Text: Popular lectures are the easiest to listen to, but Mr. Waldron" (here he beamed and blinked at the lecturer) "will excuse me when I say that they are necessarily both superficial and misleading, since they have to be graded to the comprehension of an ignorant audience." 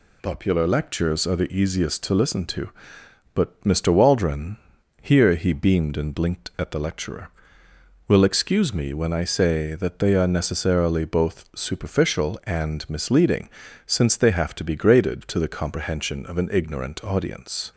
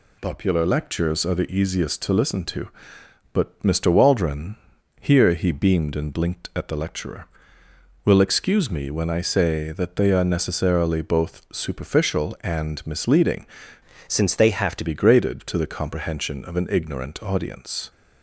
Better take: first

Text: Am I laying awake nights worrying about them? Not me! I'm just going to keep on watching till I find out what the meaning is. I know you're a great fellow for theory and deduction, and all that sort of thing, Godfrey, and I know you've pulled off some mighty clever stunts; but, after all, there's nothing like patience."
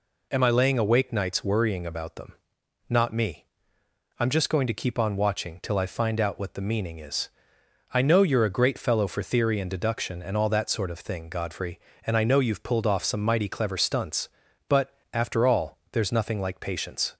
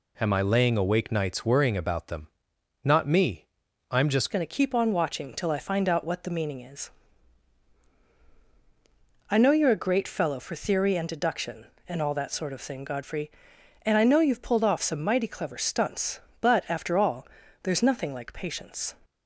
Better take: first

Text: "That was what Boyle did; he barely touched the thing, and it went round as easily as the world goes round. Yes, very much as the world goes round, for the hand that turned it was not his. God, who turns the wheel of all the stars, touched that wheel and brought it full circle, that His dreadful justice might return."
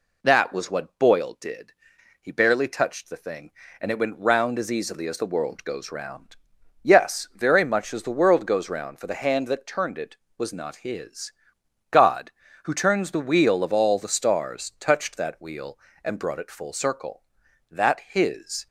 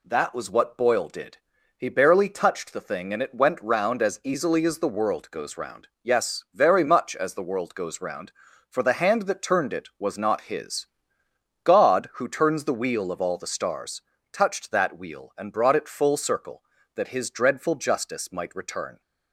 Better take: second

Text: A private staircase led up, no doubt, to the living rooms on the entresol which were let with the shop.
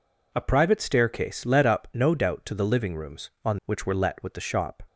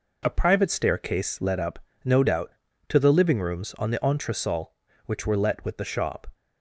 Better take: second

